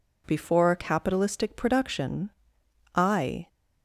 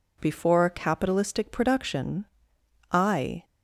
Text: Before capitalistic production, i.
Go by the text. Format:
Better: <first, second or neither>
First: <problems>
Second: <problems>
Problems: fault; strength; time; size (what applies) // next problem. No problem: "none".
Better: neither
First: none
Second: none